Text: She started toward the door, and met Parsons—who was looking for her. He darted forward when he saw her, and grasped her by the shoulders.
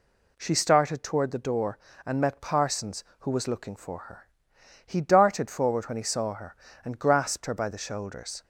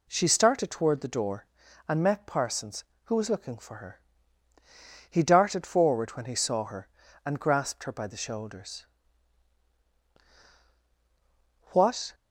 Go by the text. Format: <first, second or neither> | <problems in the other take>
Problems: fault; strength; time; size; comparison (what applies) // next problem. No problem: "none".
first | goes on to say "What"; slight; from 11.7 s on; 0.42 s long